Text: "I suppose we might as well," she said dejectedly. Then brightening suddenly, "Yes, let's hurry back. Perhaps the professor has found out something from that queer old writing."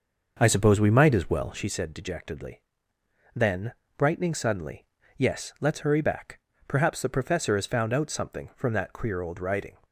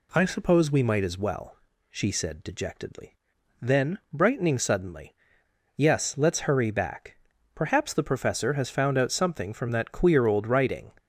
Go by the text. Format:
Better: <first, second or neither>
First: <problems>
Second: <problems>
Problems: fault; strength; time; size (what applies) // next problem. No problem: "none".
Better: second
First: starts louder than the rest; noticeable; until 1.7 s; 6 dB // pauses between "Then" and "brightening"; slight; at 3.7 s; 0.24 s long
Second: none